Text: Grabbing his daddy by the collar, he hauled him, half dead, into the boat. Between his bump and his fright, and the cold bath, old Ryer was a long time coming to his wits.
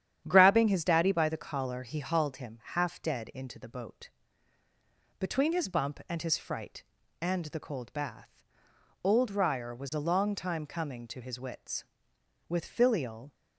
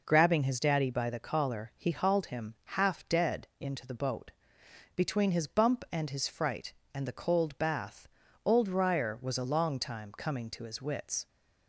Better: second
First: starts louder than the rest; strong; until 1.2 s; 9.5 dB // goes on to say "With filial"; noticeable; from 12.4 s on; 0.86 s long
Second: none

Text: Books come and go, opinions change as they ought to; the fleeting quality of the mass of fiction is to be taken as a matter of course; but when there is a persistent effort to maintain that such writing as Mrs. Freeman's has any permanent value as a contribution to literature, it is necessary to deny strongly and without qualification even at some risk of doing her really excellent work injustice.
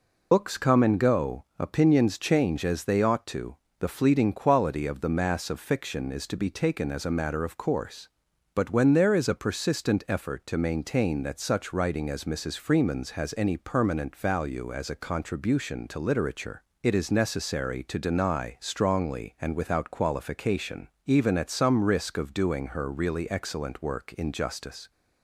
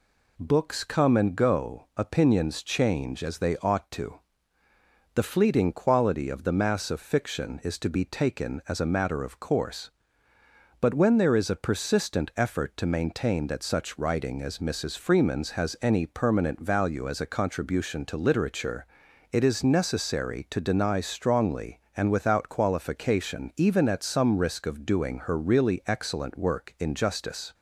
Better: second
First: loses the start of "Books"; at 0.3 s; 100 ms // pauses between "qualification" and "even"; slight; at 20.8 s; 0.18 s long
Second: none

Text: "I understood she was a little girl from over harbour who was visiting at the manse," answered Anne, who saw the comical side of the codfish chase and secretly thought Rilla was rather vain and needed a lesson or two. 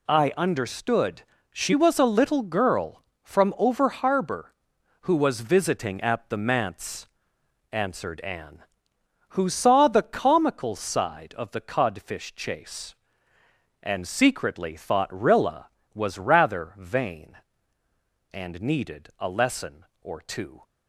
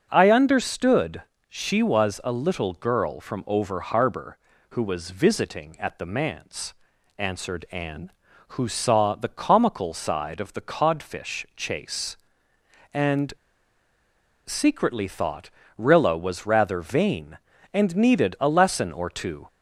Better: first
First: pauses between "understood" and "she"; slight; at 1.2 s; 0.28 s long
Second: pauses between "understood" and "she"; slight; at 1.2 s; 0.28 s long // pauses between "and" and "secretly"; at 13.3 s; 1.1 s long // pauses between "thought" and "Rilla"; slight; at 15.5 s; 0.26 s long

